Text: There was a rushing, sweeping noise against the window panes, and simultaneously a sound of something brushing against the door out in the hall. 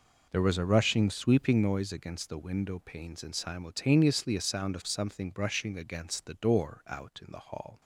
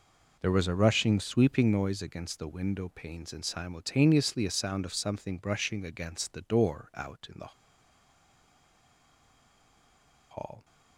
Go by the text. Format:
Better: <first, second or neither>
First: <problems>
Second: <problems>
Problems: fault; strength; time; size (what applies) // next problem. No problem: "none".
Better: first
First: none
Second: pauses between "the" and "hall"; strong; at 7.5 s; 2.7 s long